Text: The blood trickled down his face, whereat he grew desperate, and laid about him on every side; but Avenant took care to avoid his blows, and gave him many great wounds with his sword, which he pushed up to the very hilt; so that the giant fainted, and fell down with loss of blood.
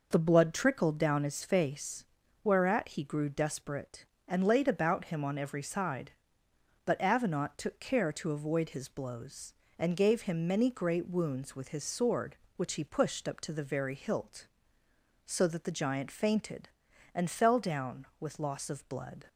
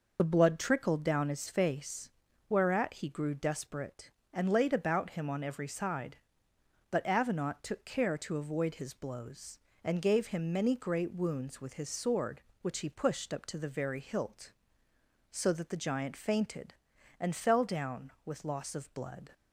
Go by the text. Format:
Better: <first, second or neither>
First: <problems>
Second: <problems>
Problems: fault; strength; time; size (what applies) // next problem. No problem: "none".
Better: first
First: none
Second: loses the start of "The"; at 0.1 s; 40 ms